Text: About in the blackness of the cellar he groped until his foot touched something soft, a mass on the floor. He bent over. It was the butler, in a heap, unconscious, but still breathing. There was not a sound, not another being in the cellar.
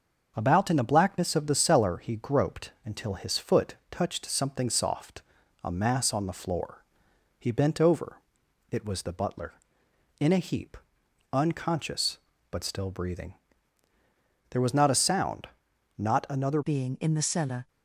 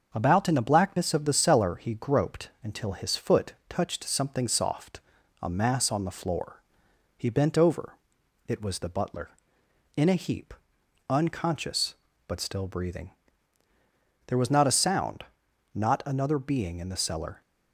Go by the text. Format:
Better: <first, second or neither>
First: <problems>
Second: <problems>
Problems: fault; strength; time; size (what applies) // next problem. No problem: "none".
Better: second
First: starts louder than the rest; until 1.3 s; 6.5 dB // pauses between "foot" and "touched"; slight; at 3.7 s; 0.16 s long // changes voice at "being"; from 16.6 s on; 1.0 s long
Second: starts louder than the rest; until 1.1 s; 6.5 dB // pauses between "foot" and "touched"; slight; at 3.5 s; 0.16 s long